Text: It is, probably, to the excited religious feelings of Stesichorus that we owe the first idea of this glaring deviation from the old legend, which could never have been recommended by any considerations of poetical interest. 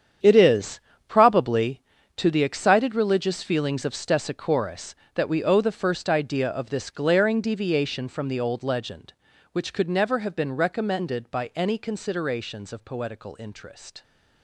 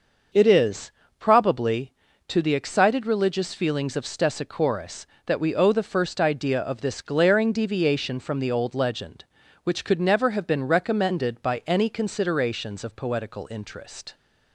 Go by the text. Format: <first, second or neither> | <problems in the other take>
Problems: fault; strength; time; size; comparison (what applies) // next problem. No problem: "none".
second | gets quieter; strong; throughout; 13 dB // starts louder than the rest; strong; until 1.5 s; 8.5 dB; also in the second